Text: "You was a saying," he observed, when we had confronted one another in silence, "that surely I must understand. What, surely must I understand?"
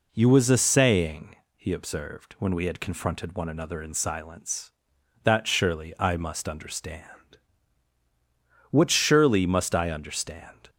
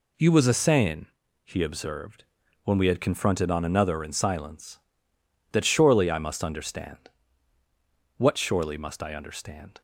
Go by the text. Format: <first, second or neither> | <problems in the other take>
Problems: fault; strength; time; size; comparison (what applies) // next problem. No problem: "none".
first | says "on" for "one"; at 3.5 s